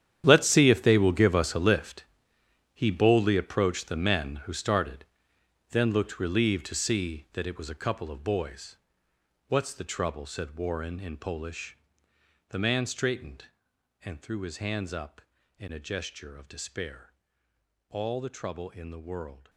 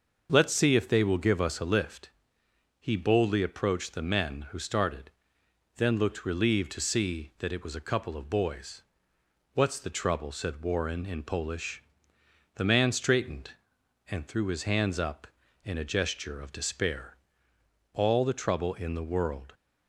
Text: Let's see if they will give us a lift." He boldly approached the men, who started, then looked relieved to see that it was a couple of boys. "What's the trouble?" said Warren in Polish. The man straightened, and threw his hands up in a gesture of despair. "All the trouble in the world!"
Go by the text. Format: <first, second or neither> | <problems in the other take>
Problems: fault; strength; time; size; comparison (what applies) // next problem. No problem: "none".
second | gets quieter; strong; throughout; 15.5 dB // starts louder than the rest; strong; until 1.2 s; 10 dB; also in the second